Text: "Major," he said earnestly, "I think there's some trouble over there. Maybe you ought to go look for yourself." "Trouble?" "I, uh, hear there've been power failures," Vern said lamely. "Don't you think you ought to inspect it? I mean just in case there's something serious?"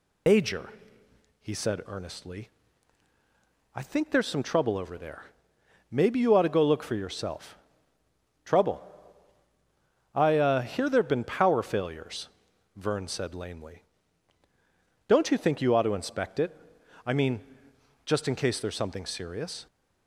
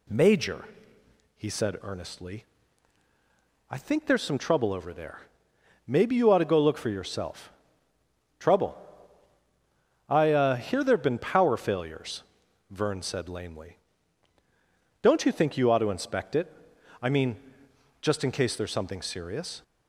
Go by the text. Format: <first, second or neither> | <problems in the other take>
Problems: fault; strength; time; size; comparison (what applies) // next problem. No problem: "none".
second | loses the start of "Major"; at 0.2 s; 145 ms // pauses between "mean" and "just"; noticeable; at 17.4 s; 0.58 s long; noticeable in the second